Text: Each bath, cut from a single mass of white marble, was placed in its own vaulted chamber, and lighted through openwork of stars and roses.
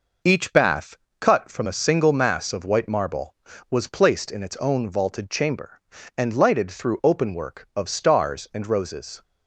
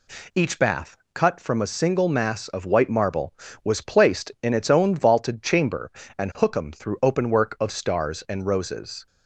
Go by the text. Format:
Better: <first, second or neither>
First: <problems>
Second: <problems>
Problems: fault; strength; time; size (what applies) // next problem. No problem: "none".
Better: first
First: none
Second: says "hookum" for "lighted"; at 6.3 s